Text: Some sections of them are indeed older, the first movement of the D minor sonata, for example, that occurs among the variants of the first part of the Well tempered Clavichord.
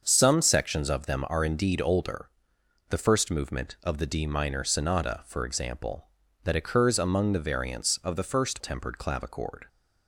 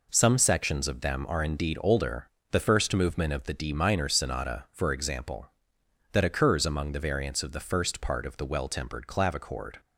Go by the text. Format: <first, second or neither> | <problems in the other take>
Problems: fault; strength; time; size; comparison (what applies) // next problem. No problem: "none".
second | starts louder than the rest; until 1.0 s; 6.5 dB // skips "part of the Well"; at 8.5 s